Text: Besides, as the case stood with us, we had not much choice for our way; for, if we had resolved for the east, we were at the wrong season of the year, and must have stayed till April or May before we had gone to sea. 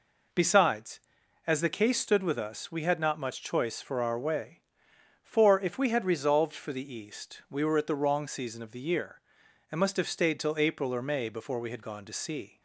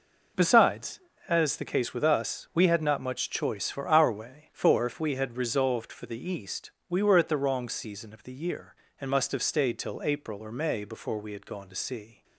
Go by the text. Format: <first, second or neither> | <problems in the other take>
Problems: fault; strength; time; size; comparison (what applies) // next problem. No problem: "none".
first | skips "stood"; at 1.9 s